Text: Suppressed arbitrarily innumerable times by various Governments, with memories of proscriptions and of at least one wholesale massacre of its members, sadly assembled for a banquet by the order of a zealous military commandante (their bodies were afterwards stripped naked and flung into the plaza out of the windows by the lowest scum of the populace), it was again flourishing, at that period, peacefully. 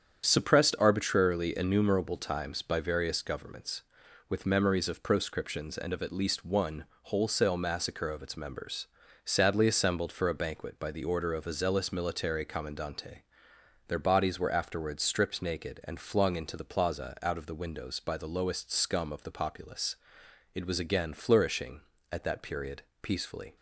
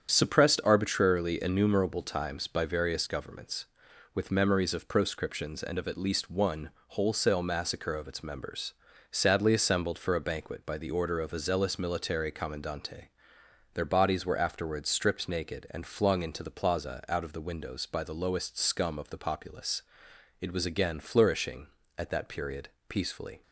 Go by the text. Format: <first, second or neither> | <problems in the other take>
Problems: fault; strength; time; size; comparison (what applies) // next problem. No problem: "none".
neither | starts louder than the rest; strong; the same in both // pauses between "one" and "wholesale"; slight; the same in both